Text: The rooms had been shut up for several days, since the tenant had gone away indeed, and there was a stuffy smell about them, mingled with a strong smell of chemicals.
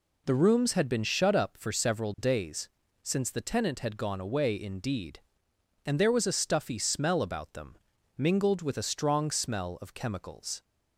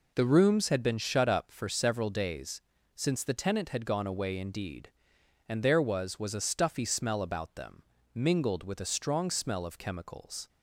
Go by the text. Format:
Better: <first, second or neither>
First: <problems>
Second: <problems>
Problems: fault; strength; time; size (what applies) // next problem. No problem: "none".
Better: first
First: none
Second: says "was" twice; at 6.1 s